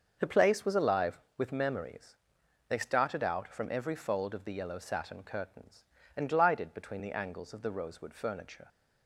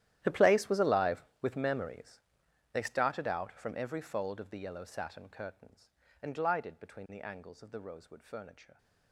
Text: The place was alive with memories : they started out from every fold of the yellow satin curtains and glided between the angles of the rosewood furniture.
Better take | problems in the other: first | gets quieter; strong; throughout; 19 dB // starts louder than the rest; strong; until 1.2 s; 12.5 dB; also in the first

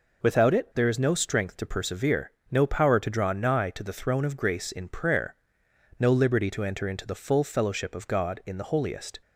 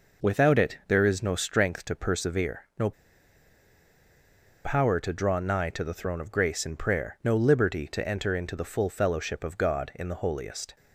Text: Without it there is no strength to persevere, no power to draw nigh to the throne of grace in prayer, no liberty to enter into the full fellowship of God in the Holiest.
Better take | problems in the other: first | pauses between "no" and "power"; strong; at 2.9 s; 1.7 s long

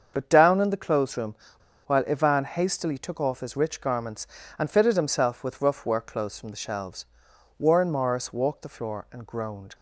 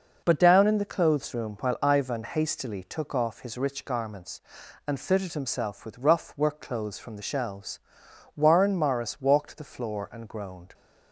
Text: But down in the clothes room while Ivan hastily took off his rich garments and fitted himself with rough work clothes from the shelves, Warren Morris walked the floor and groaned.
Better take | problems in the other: second | starts louder than the rest; until 1.1 s; 7 dB // pauses between "room" and "while"; noticeable; at 1.3 s; 0.51 s long

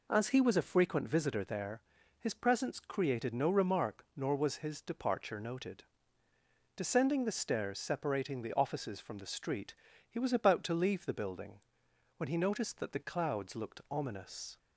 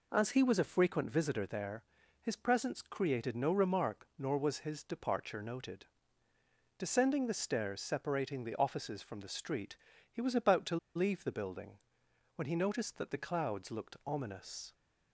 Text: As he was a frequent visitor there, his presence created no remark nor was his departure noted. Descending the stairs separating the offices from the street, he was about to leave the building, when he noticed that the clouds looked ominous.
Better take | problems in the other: first | pauses between "to" and "leave"; slight; at 10.7 s; 0.18 s long

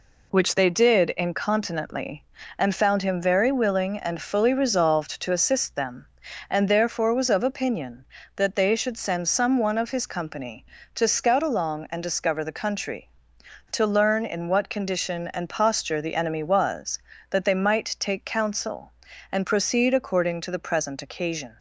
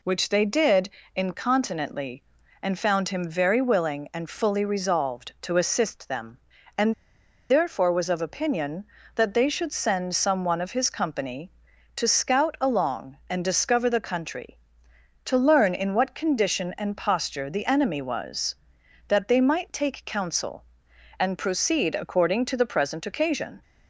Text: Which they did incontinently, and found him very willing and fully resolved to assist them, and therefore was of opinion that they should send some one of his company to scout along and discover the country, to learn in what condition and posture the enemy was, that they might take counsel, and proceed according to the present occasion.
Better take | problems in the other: first | pauses between "did" and "incontinently"; slight; at 0.8 s; 0.26 s long // pauses between "and" and "therefore"; noticeable; at 6.9 s; 0.57 s long

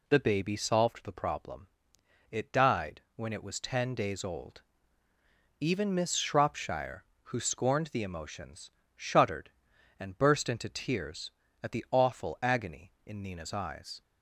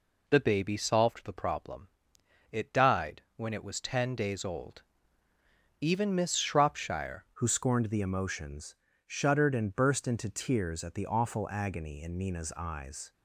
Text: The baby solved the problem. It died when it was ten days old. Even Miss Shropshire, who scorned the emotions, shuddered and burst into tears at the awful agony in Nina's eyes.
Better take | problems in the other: first | changes voice at "who"; from 7.3 s on; 5.8 s long

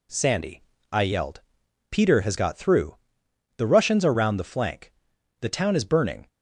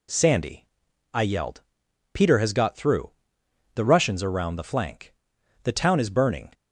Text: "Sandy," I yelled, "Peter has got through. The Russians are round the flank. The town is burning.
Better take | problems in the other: neither | none

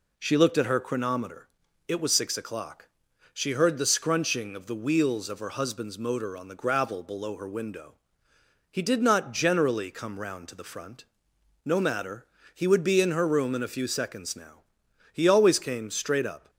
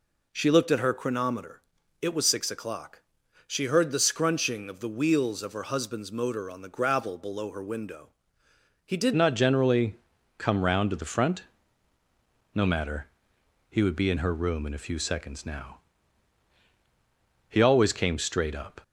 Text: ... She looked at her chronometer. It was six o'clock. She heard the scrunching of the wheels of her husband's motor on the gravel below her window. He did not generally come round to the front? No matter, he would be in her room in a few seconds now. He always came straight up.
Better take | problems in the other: first | changes voice at "not"; from 9.1 s on; 9.7 s long // pauses between "generally" and "come"; at 9.9 s; 0.44 s long

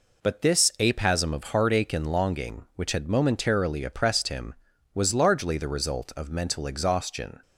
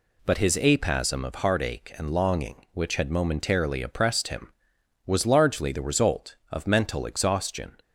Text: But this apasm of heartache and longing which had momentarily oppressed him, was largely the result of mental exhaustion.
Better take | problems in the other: first | says "his" for "this"; at 0.3 s

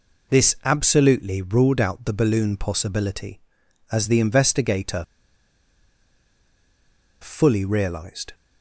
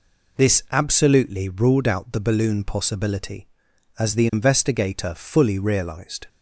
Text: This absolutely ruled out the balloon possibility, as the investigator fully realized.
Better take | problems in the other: second | pauses between "investigator" and "fully"; strong; at 5.0 s; 2.1 s long

